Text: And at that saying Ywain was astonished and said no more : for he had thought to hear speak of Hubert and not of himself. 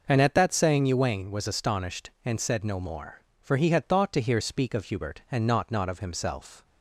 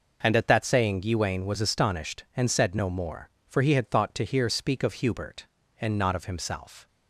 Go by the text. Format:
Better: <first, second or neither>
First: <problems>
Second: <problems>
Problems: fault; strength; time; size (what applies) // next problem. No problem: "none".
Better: second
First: says "not" twice; at 5.7 s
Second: none